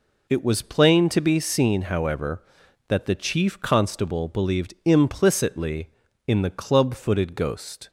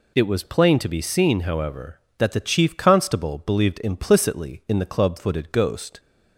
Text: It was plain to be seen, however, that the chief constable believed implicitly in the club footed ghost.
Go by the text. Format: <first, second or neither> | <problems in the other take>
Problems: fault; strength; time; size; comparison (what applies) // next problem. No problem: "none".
neither | none